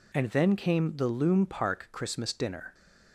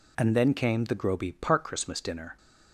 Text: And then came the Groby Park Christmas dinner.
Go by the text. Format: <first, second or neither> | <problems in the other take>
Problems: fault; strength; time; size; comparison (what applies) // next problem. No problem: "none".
second | says "Loom" for "Groby"; at 1.0 s